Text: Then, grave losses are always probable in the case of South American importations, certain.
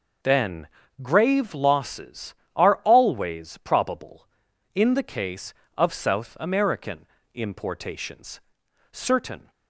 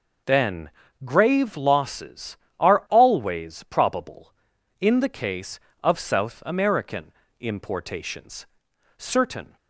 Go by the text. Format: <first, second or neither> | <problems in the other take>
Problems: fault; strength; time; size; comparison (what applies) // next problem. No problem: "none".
neither | pauses between "American" and "importations"; slight; the same in both